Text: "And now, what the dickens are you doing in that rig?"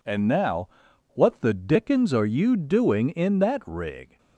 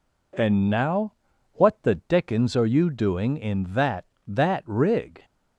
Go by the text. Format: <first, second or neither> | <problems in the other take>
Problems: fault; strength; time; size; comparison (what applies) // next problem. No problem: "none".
first | says "that" twice; at 4.2 s